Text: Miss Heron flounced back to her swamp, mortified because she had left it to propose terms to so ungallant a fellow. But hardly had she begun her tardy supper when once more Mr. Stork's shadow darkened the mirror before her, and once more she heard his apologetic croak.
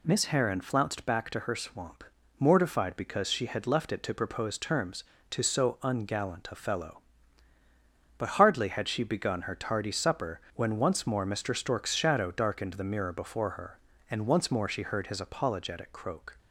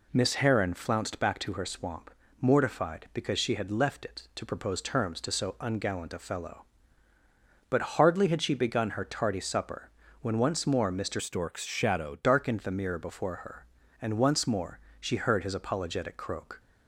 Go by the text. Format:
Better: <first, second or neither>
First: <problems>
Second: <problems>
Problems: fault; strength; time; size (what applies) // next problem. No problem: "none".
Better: first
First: pauses between "supper" and "when"; slight; at 10.4 s; 0.16 s long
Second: pauses between "supper" and "when"; slight; at 9.9 s; 0.32 s long // changes voice from "Stork's" to "shadow"; from 11.1 to 12.1 s; 1.0 s long // pauses between "more" and "she"; slight; at 14.7 s; 0.20 s long